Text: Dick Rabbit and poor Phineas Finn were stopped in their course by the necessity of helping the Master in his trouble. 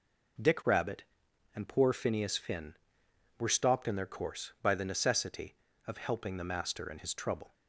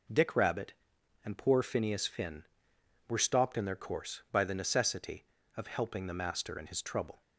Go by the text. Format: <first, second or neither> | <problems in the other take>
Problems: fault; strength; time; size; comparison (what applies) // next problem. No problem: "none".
neither | none